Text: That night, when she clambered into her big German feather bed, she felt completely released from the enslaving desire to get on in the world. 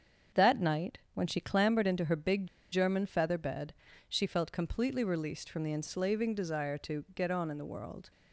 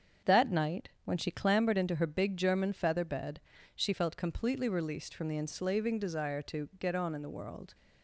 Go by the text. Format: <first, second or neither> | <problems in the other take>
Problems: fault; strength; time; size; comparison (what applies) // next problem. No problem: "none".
second | starts louder than the rest; strong; until 1.5 s; 7 dB; also in the second // pauses between "big" and "German"; slight; at 2.4 s; 0.25 s long